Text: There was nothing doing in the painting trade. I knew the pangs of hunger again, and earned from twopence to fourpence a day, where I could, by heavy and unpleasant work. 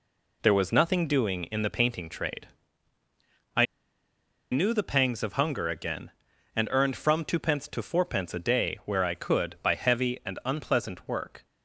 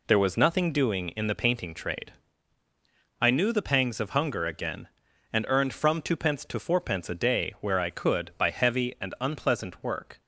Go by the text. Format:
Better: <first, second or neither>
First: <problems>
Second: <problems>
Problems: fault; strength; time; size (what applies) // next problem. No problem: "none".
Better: second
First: pauses between "I" and "knew"; noticeable; at 3.6 s; 0.86 s long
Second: none